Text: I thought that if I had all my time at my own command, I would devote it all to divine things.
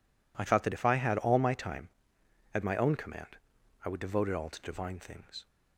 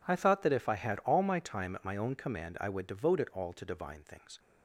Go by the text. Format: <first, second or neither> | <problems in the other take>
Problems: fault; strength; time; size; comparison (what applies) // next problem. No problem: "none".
neither | none